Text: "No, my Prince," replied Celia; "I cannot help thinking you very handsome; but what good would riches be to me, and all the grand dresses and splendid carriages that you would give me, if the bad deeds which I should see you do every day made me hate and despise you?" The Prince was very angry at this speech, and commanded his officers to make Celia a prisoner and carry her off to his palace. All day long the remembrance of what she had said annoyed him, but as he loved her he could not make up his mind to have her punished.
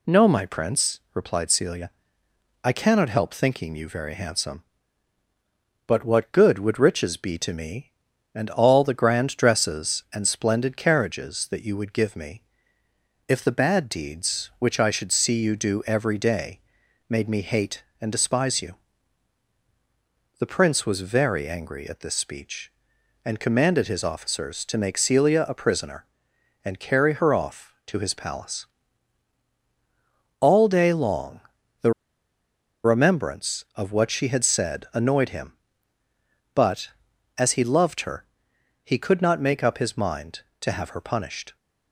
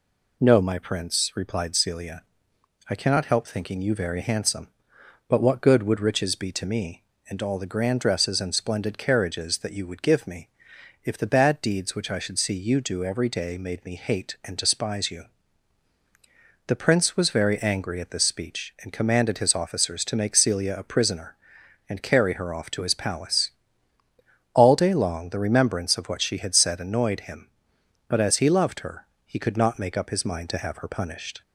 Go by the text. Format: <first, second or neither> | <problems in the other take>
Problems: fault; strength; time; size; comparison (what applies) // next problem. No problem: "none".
second | pauses between "day" and "made"; noticeable; at 16.5 s; 0.48 s long // pauses between "long" and "the"; at 31.3 s; 0.40 s long // pauses between "the" and "remembrance"; noticeable; at 31.9 s; 0.92 s long // pauses between "her" and "he"; noticeable; at 38.2 s; 0.60 s long; slight in the second